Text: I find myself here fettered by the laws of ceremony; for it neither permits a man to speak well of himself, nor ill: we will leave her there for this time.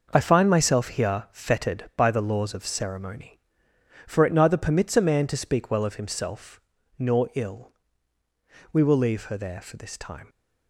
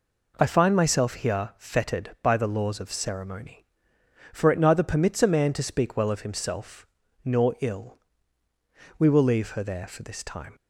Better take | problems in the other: second | gets quieter; strong; throughout; 9 dB

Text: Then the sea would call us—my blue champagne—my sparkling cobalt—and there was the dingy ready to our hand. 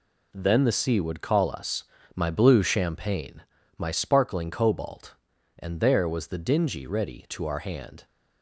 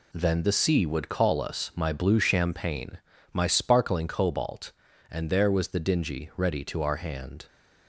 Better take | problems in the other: neither | none

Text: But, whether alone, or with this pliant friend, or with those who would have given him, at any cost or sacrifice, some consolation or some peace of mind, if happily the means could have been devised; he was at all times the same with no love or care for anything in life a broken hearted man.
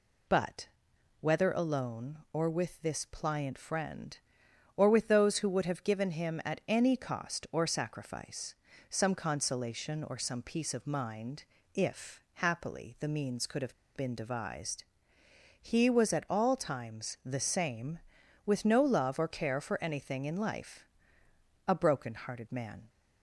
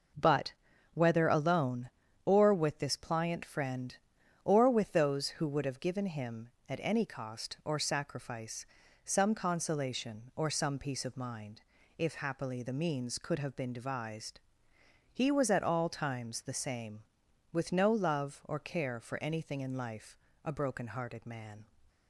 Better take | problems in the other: second | pauses between "have" and "been"; slight; at 13.7 s; 0.21 s long // pauses between "life" and "a"; noticeable; at 20.8 s; 0.84 s long; slight in the second

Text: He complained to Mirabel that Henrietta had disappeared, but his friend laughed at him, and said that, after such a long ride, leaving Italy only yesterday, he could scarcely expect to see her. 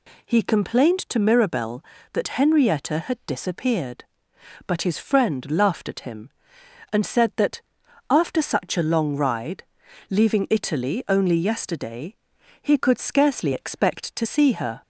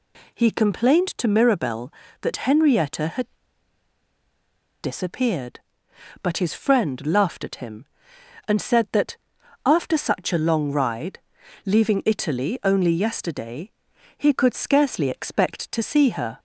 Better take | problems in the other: first | pauses between "had" and "disappeared"; strong; at 3.2 s; 1.5 s long

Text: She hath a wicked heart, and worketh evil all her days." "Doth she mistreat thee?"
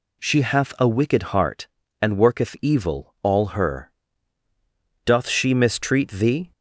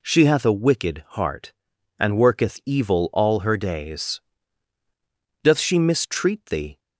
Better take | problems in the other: second | skips "days"; at 4.4 s

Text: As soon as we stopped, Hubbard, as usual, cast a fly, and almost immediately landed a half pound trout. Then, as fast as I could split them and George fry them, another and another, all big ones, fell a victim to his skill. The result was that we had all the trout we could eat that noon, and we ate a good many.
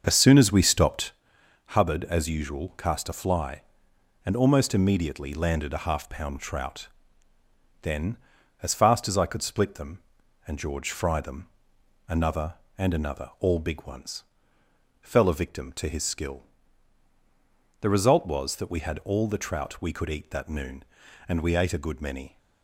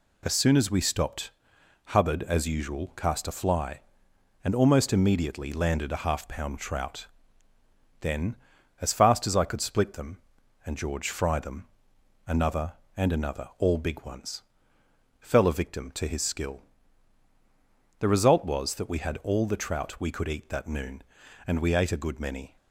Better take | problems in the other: second | starts louder than the rest; until 1.3 s; 6.5 dB

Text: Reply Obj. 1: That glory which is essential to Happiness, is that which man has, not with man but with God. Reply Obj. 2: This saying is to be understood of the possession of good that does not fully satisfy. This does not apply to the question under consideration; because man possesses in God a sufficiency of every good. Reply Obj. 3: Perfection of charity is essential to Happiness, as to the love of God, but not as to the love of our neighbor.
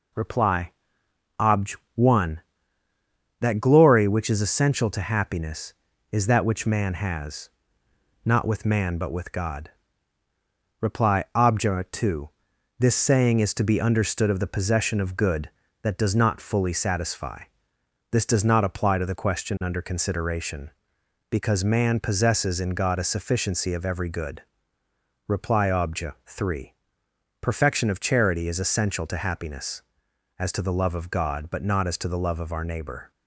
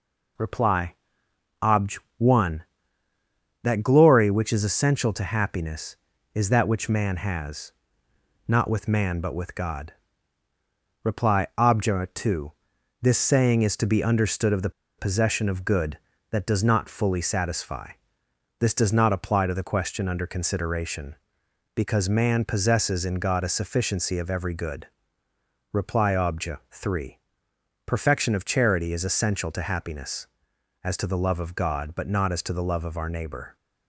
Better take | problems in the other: first | pauses between "Reply" and "Obj"; noticeable; at 0.9 s; 0.66 s long; noticeable in the first // pauses between "the" and "possession"; slight; at 14.6 s; 0.28 s long

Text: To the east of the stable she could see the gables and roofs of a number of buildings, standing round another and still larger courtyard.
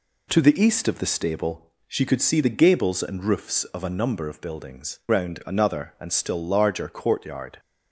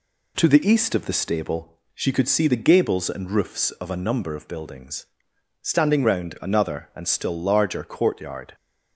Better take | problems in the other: second | pauses between "stable" and "she"; slight; at 1.7 s; 0.16 s long; slight in the second // skips "standing"; at 5.0 s

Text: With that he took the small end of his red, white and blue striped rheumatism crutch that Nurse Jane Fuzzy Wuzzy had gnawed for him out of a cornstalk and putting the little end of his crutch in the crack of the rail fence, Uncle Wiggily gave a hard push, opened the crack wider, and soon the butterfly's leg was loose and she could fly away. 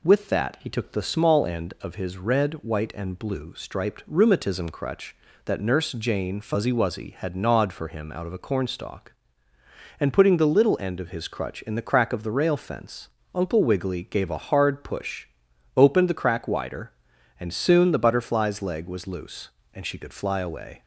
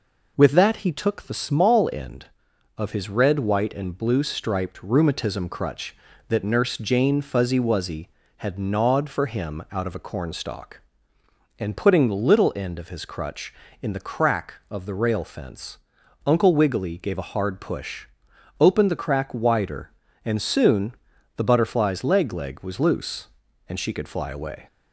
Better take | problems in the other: first | pauses between "soon" and "the"; at 20.9 s; 0.44 s long // says "leg" twice; at 22.3 s

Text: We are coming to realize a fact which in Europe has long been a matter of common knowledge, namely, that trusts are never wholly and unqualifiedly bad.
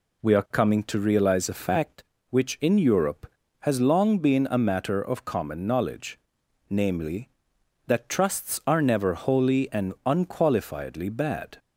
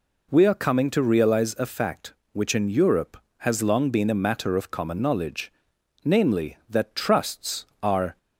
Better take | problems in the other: first | stops before "never wholly and unqualifiedly bad"; at 8.1 s

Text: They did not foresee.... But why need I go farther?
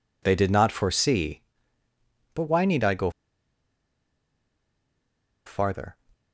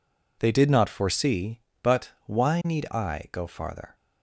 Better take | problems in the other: second | pauses between "go" and "farther"; strong; at 3.1 s; 2.3 s long

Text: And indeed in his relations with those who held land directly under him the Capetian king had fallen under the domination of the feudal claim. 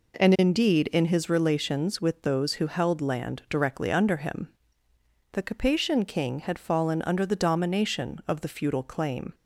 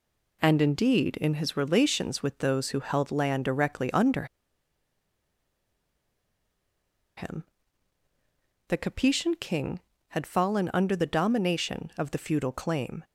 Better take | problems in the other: first | pauses between "under" and "him"; strong; at 4.2 s; 2.9 s long // pauses between "him" and "the"; at 7.4 s; 1.2 s long; noticeable in the first

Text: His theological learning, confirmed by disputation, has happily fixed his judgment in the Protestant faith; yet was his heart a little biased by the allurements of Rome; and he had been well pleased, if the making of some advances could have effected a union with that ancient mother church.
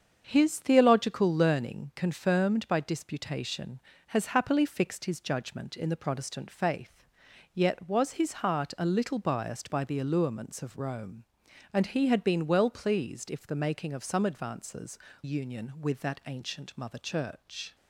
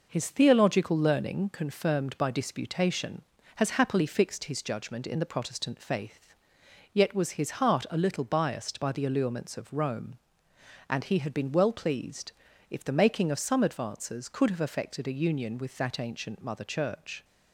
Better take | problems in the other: second | starts louder than the rest; strong; until 1.2 s; 7.5 dB // skips "could have effected a"; at 15.0 s

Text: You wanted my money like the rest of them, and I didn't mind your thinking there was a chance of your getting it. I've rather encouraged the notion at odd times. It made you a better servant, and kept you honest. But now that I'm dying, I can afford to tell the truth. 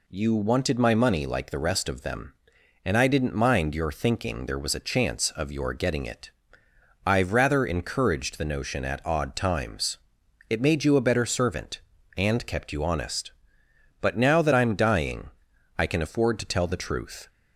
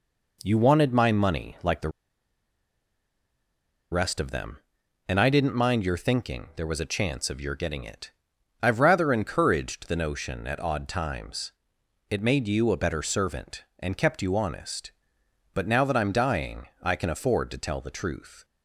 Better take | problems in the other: first | pauses between "the" and "rest"; strong; at 1.8 s; 2.0 s long

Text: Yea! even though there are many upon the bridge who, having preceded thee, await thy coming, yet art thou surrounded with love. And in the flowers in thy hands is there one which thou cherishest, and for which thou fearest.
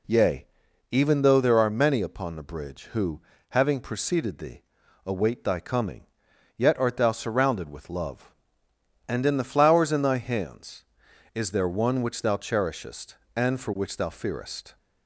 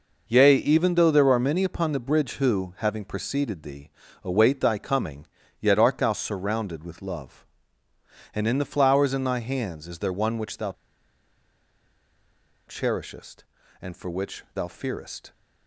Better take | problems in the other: first | pauses between "thou" and "cherishest"; strong; at 10.7 s; 1.9 s long

